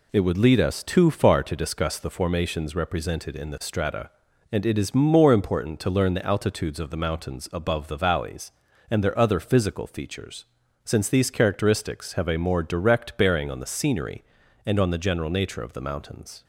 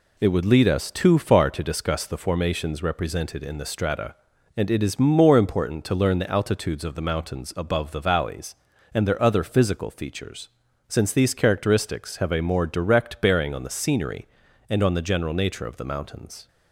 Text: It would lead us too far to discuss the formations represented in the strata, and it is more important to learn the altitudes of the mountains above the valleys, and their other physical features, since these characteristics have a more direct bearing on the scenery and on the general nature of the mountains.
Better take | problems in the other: neither | none

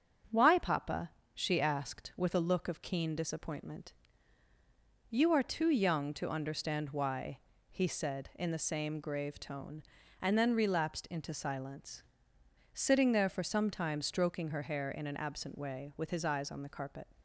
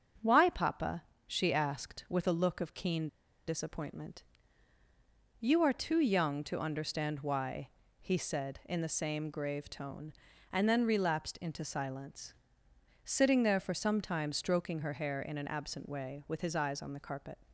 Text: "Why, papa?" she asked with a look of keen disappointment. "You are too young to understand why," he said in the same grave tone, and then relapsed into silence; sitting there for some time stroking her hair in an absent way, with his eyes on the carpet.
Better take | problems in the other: first | starts louder than the rest; strong; until 1.4 s; 7 dB; strong in the first // pauses between "keen" and "disappointment"; at 3.0 s; 0.40 s long

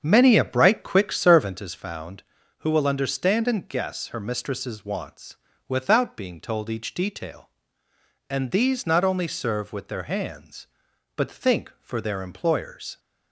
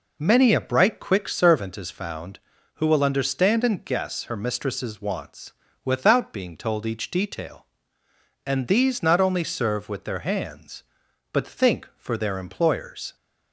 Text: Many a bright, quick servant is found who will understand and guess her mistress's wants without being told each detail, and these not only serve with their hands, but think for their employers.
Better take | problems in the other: second | starts louder than the rest; strong; until 1.8 s; 7.5 dB // pauses between "wants" and "without"; slight; at 5.3 s; 0.32 s long; slight in the second

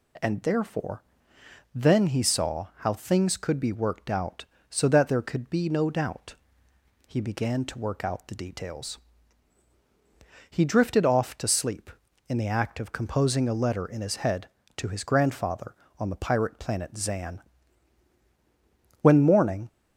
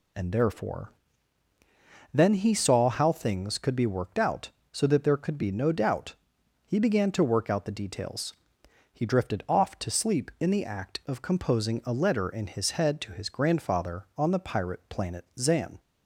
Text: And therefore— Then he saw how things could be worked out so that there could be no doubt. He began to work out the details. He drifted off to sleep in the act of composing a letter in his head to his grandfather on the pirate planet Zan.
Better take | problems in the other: second | goes on to say "When morning"; noticeable; from 19.0 s on; 0.66 s long

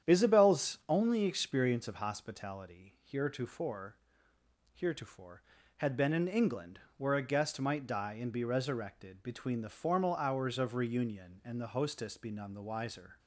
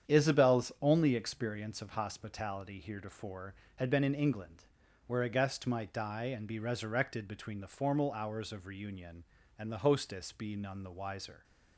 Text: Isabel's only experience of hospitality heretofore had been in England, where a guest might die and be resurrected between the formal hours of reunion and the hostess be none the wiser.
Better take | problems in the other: second | starts louder than the rest; strong; until 1.1 s; 9 dB; strong in the second // says "heretofore" twice; at 4.7 s

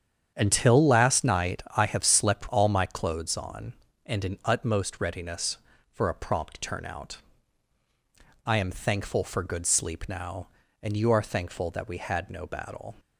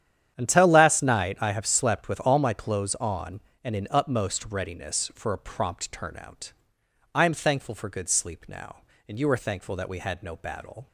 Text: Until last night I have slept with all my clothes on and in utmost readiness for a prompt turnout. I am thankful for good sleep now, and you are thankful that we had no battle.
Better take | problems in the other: second | starts louder than the rest; strong; until 1.3 s; 8.5 dB; strong in the second // skips "with"; at 2.4 s

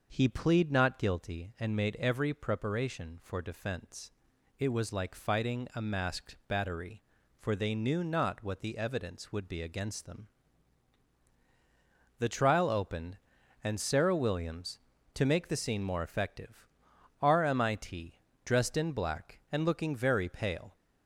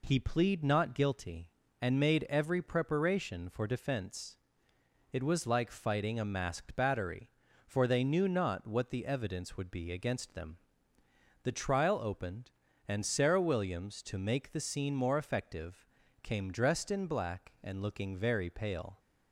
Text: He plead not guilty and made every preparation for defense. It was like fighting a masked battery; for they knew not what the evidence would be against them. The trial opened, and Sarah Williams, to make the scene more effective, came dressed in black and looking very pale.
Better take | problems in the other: second | starts louder than the rest; noticeable; until 1.1 s; 6 dB // says "rmit" for "came"; at 17.2 s

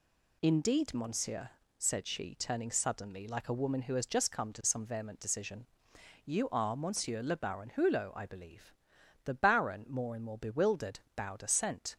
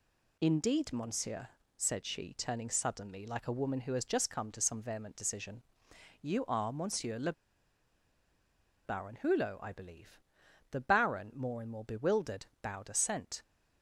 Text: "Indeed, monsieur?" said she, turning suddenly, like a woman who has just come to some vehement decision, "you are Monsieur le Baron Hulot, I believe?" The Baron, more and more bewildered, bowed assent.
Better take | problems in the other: first | pauses between "le" and "Baron"; strong; at 7.3 s; 1.5 s long

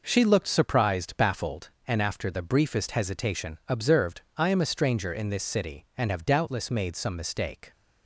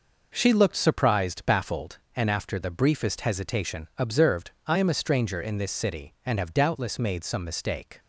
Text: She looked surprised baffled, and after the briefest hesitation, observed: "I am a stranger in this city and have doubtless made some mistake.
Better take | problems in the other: neither | none

